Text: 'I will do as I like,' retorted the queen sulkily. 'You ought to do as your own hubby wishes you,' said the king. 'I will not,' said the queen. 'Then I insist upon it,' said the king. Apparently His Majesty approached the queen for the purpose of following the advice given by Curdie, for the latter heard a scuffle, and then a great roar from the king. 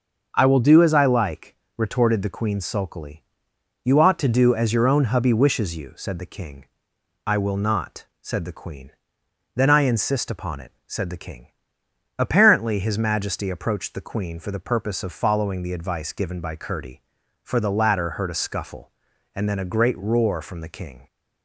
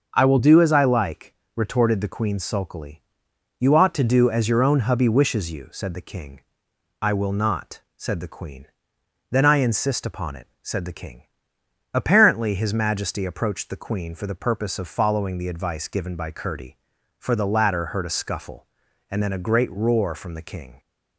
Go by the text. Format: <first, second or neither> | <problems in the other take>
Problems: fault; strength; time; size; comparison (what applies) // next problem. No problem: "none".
neither | starts louder than the rest; the same in both